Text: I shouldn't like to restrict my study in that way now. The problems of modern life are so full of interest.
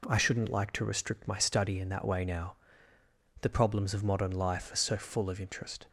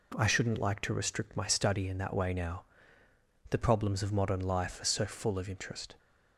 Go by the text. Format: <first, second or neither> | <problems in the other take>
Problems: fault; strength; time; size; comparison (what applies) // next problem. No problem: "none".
neither | none